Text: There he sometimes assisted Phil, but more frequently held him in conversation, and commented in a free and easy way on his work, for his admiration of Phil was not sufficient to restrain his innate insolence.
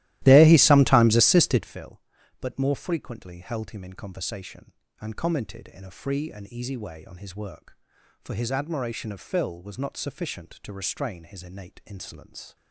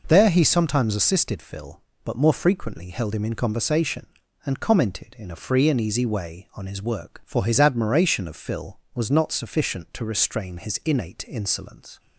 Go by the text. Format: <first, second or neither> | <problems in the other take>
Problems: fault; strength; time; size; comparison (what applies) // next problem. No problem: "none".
second | starts louder than the rest; strong; until 1.8 s; 16 dB